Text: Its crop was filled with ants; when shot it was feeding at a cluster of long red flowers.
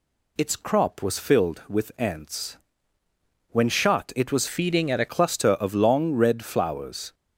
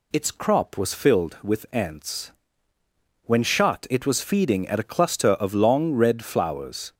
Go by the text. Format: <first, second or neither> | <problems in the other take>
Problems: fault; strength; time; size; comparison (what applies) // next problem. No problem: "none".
second | changes voice from "feeding" to "a"; from 4.4 to 5.0 s; 0.6 s long